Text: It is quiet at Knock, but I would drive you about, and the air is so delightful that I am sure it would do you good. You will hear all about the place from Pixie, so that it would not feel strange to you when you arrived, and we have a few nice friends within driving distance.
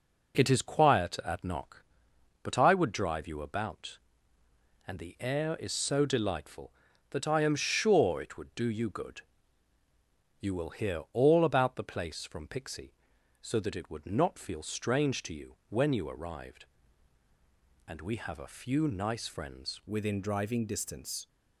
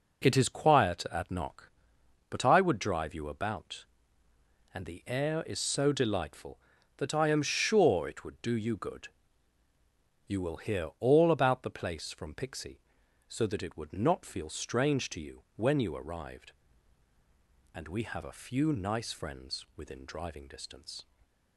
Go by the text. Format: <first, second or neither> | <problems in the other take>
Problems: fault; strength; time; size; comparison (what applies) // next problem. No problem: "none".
second | changes voice at "within"; from 19.8 s on; 1.4 s long